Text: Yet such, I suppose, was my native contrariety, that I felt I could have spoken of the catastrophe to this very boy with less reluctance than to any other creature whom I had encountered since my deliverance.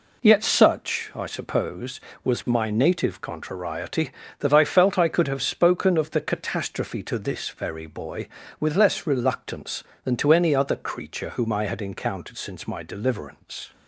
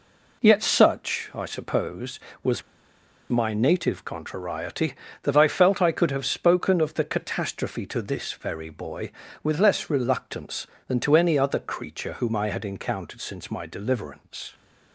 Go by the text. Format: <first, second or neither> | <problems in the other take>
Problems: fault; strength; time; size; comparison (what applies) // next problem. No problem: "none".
first | pauses between "was" and "my"; noticeable; at 2.6 s; 0.69 s long